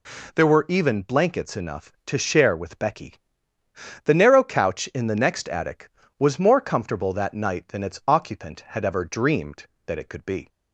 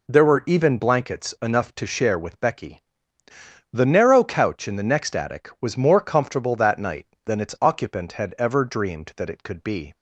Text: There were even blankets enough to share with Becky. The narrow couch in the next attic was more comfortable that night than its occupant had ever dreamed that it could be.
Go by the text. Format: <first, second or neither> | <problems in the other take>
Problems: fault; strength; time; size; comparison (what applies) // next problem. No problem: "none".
neither | none